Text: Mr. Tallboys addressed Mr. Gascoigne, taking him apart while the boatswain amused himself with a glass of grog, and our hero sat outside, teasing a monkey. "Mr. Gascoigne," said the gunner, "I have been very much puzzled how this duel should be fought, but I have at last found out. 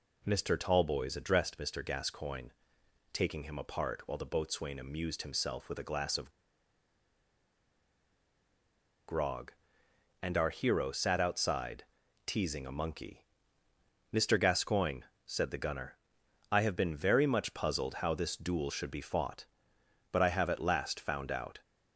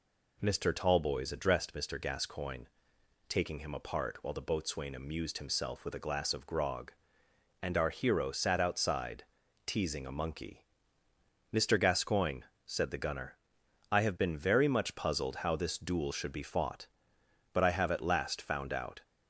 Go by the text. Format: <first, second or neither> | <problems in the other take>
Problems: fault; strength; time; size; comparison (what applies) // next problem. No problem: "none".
second | pauses between "of" and "grog"; strong; at 6.3 s; 2.7 s long